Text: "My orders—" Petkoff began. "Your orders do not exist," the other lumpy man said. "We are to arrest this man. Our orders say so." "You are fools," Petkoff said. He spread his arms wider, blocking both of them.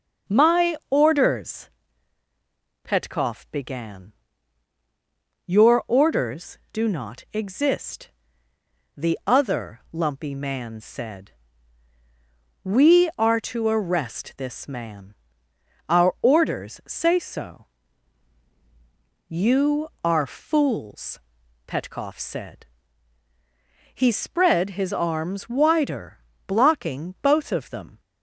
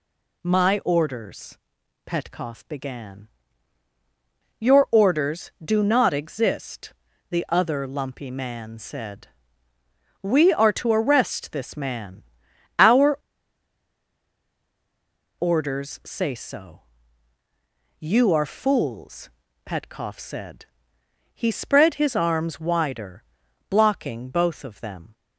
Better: first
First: none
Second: pauses between "Our" and "orders"; strong; at 13.1 s; 2.1 s long

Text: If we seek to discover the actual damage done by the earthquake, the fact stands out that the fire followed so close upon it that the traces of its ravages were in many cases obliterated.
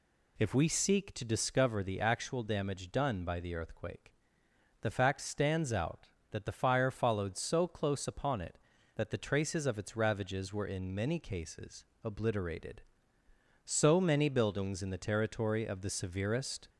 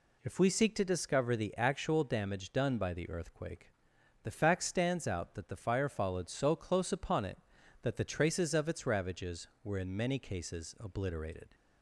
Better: second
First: pauses between "cases" and "obliterated"; slight; at 11.8 s; 0.20 s long // goes on to say "So many buildings in the territory of the severest"; strong; from 13.6 s on; 3.0 s long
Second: none

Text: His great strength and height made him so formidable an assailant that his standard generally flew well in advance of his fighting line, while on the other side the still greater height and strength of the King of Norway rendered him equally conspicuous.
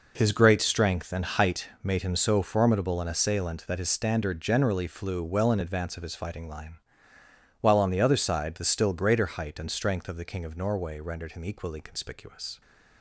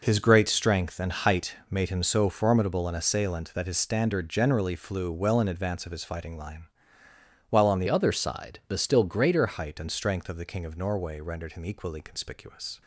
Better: first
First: pauses between "height" and "made"; slight; at 1.6 s; 0.16 s long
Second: pauses between "height" and "made"; slight; at 1.5 s; 0.16 s long // changes voice from "other" to "greater"; from 7.8 to 9.4 s; 1.6 s long

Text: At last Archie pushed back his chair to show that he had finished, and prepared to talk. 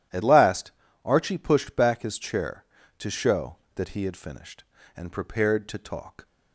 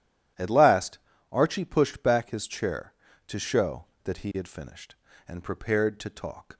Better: neither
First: pauses between "last" and "Archie"; slight; at 0.7 s; 0.32 s long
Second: pauses between "last" and "Archie"; slight; at 0.9 s; 0.32 s long

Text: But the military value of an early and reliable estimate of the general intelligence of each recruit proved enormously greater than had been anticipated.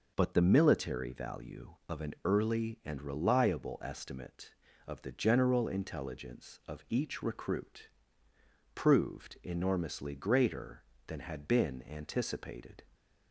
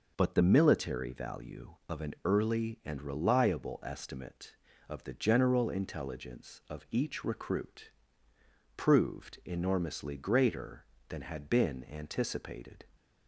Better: neither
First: pauses between "recruit" and "proved"; noticeable; at 7.8 s; 0.86 s long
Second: pauses between "recruit" and "proved"; noticeable; at 7.8 s; 0.86 s long

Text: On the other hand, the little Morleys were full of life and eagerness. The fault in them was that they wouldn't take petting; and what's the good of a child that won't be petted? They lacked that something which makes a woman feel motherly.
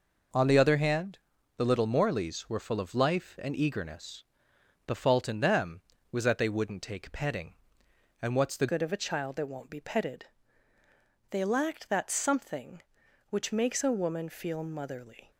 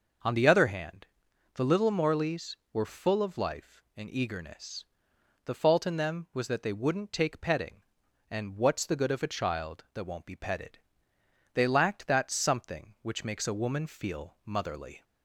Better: second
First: changes voice at "good"; from 8.7 s on; 6.6 s long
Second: none

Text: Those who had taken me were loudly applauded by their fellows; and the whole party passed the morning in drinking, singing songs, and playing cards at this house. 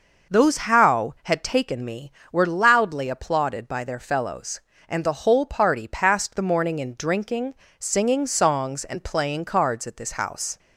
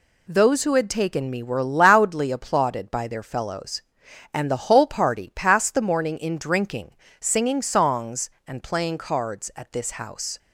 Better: second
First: says "how" for "who"; at 0.5 s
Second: none

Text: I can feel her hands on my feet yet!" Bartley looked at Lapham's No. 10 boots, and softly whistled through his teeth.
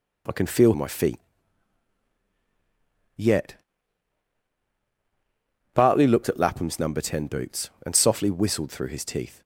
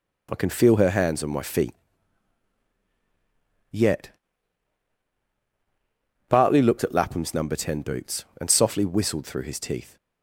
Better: second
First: skips "her hands on"; at 0.7 s // pauses between "feet" and "yet"; strong; at 1.1 s; 1.9 s long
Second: pauses between "feet" and "yet"; strong; at 1.7 s; 1.9 s long

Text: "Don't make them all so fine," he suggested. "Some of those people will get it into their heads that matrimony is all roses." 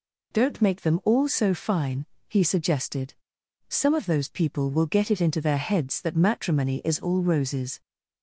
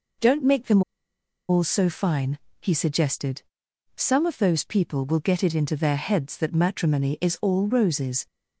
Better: first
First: none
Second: pauses between "them" and "all"; noticeable; at 0.8 s; 0.66 s long

